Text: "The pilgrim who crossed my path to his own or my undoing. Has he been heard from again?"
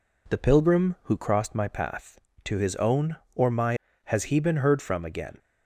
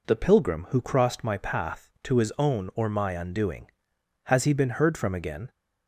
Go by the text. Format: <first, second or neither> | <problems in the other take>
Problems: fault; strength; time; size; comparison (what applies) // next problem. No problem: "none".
second | skips "undoing"; at 3.8 s